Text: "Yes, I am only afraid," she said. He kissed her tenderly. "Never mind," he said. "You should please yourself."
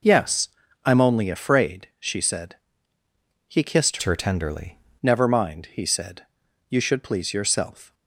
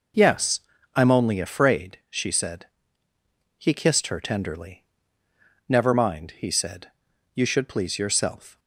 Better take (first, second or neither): second